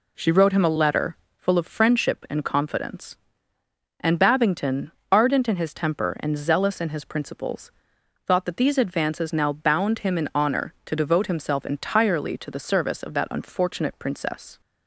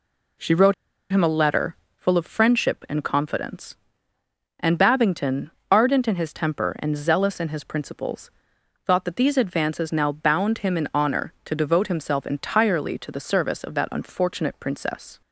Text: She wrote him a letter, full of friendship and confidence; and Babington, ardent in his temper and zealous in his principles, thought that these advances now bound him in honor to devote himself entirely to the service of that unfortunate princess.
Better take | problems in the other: first | pauses between "wrote" and "him"; at 0.7 s; 0.38 s long

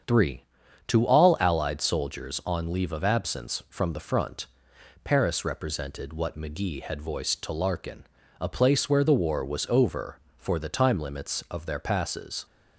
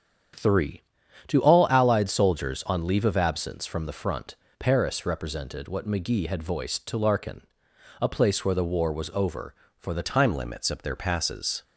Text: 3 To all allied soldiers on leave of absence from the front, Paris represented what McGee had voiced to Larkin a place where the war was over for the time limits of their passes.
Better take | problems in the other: first | starts louder than the rest; strong; until 1.8 s; 8.5 dB; strong in the first // pauses between "Larkin" and "a"; noticeable; at 7.4 s; 0.58 s long; slight in the first // changes voice at "time"; from 10.0 s on; 1.6 s long

